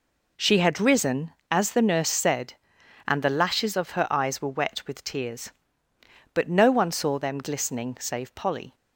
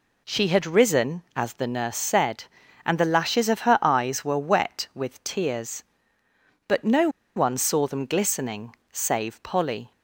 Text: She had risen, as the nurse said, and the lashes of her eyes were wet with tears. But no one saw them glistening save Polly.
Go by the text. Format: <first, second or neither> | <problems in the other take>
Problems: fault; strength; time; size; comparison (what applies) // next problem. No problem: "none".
first | pauses between "no" and "one"; slight; at 7.0 s; 0.26 s long // pauses between "glistening" and "save"; slight; at 8.7 s; 0.16 s long